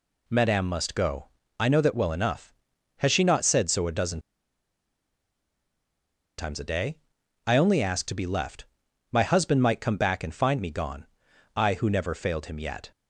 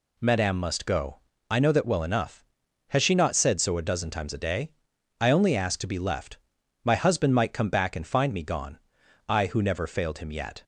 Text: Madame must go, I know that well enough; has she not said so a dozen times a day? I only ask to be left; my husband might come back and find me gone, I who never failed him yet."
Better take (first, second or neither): second